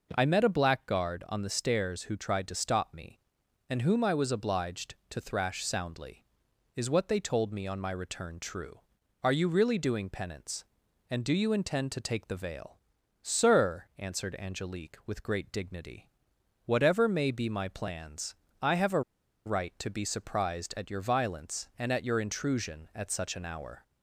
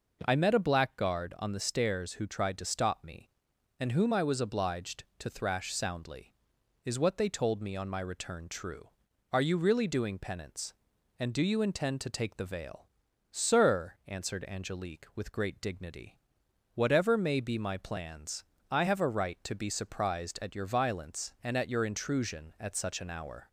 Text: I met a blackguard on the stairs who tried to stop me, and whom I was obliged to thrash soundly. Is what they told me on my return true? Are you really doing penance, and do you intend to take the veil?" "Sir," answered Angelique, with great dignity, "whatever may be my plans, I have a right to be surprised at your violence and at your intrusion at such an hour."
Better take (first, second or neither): second